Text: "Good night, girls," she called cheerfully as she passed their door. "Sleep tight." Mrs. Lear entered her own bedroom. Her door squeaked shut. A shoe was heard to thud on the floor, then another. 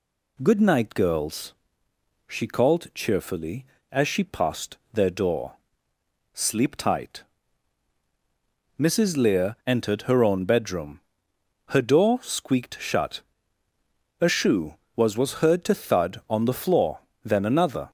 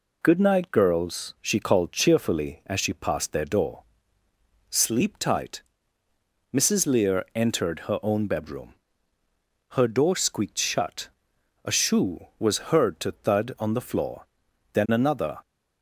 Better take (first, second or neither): second